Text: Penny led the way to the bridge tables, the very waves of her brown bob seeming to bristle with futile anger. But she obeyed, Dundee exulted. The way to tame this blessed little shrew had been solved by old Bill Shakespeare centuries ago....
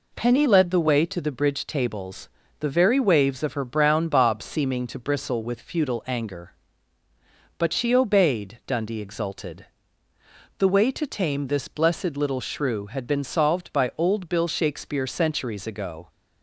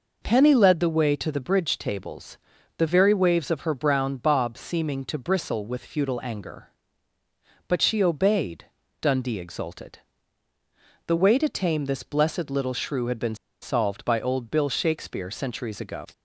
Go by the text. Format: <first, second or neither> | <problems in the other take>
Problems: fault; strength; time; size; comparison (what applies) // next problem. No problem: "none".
first | pauses between "been" and "solved"; slight; at 13.3 s; 0.27 s long